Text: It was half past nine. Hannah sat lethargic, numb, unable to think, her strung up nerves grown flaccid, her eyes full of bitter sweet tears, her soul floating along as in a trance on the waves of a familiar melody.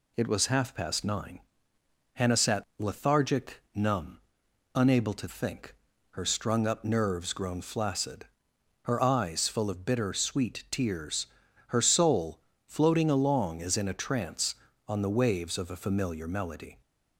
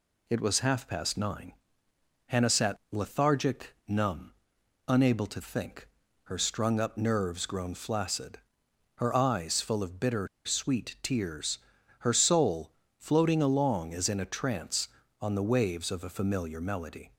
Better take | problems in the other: first | pauses between "bitter" and "sweet"; slight; at 10.2 s; 0.18 s long // pauses between "soul" and "floating"; slight; at 12.6 s; 0.28 s long; slight in the first

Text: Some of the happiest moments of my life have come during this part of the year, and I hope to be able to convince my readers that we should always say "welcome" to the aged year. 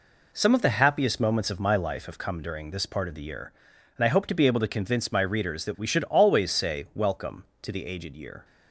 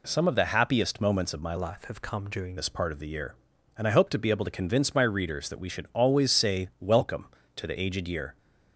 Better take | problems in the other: first | changes voice from "life" to "during"; from 1.5 to 2.5 s; 1.0 s long

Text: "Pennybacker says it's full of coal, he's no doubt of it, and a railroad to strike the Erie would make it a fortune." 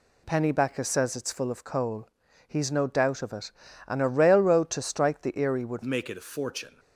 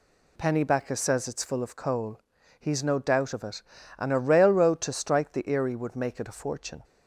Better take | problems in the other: second | changes voice at "make"; from 5.8 s on; 0.9 s long

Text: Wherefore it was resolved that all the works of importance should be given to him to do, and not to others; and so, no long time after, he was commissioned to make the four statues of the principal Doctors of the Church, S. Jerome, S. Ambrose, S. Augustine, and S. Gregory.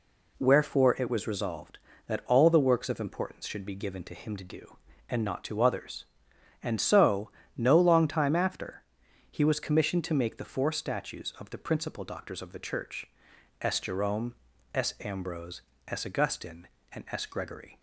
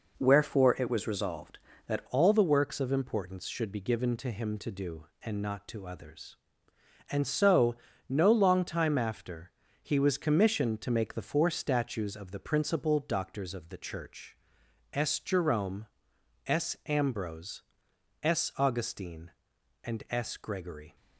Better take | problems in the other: first | changes voice at "all"; from 2.0 s on; 18.9 s long

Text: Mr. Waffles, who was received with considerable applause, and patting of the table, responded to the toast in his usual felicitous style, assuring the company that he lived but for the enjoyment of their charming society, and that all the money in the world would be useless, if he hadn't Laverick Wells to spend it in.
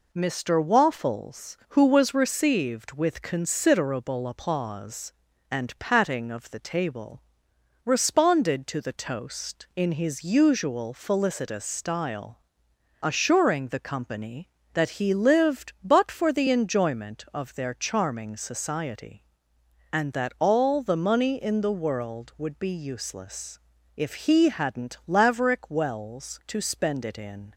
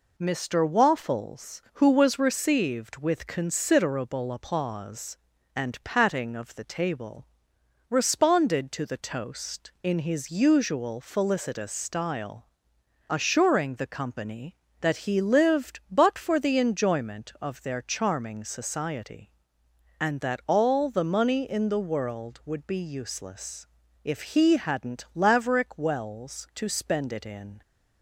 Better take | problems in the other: neither | none

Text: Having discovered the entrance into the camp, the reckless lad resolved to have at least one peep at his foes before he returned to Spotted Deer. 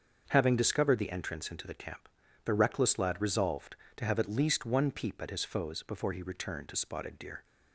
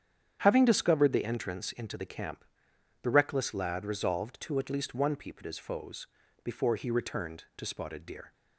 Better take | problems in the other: first | starts louder than the rest; strong; until 1.4 s; 8.5 dB; also in the first // skips "have"; at 4.5 s // pauses between "foes" and "before"; slight; at 6.0 s; 0.36 s long

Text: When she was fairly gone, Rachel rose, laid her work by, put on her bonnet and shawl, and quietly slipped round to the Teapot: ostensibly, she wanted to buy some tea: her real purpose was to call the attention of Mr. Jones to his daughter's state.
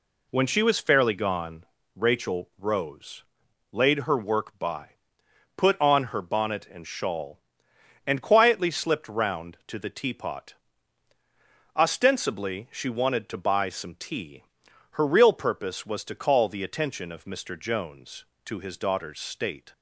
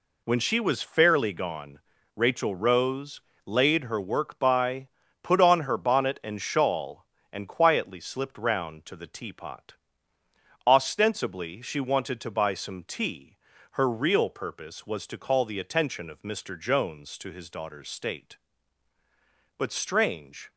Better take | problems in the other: first | goes on to say "But strange"; noticeable; from 19.5 s on; 0.92 s long

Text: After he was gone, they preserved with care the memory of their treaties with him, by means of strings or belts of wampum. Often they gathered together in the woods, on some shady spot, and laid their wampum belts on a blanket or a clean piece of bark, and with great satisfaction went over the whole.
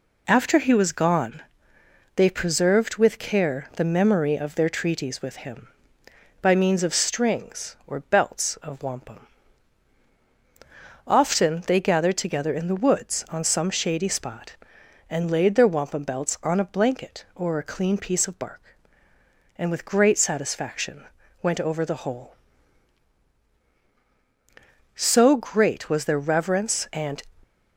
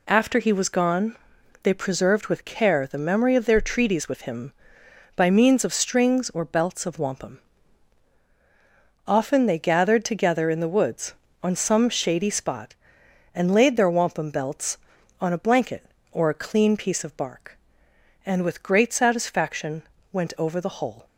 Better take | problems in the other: second | pauses between "satisfaction" and "went"; at 21.0 s; 0.40 s long; slight in the second // goes on to say "So great was their reverence and"; strong; from 24.9 s on; 2.2 s long

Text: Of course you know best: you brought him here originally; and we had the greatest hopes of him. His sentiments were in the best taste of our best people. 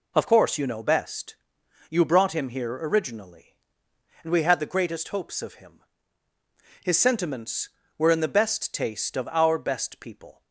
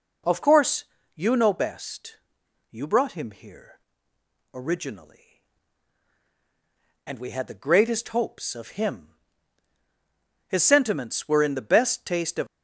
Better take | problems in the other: first | pauses between "course" and "you"; slight; at 0.8 s; 0.30 s long // pauses between "here" and "originally"; noticeable; at 3.7 s; 0.76 s long // stops before "our best people"; at 12.4 s

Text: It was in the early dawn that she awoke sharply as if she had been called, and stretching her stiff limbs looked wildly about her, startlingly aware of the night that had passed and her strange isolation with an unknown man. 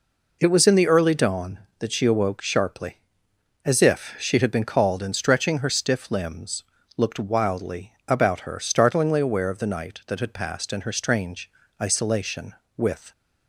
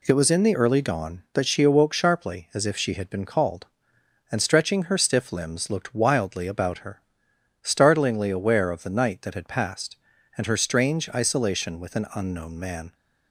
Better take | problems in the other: second | pauses between "limbs" and "looked"; slight; at 6.6 s; 0.32 s long // pauses between "wildly" and "about"; slight; at 7.9 s; 0.16 s long // pauses between "strange" and "isolation"; slight; at 11.4 s; 0.32 s long // stops before "an unknown man"; at 13.1 s

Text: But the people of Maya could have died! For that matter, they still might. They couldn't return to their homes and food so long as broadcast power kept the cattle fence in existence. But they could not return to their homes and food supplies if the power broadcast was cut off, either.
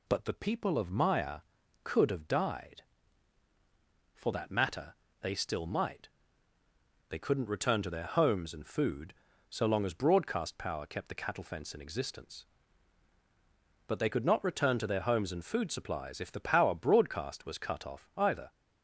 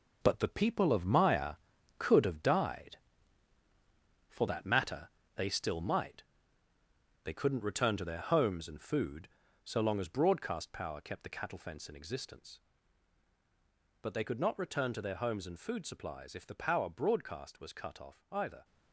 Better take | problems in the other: first | gets quieter; strong; throughout; 9 dB

